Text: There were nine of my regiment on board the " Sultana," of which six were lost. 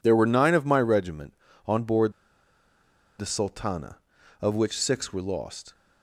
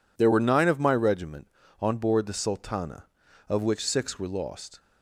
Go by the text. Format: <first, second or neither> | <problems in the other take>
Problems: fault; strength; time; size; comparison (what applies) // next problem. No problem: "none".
second | pauses between "board" and "the"; at 2.1 s; 1.0 s long